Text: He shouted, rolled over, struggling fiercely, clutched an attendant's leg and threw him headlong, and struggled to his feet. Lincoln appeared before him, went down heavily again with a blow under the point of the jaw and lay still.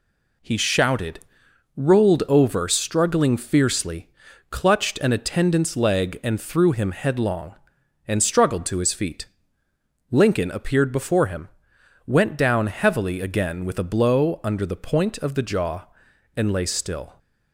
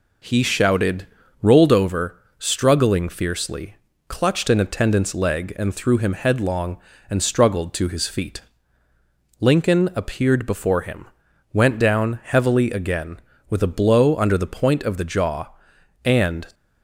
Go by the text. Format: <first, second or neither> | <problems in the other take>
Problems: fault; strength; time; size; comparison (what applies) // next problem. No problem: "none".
first | stops before "lay still"; at 16.5 s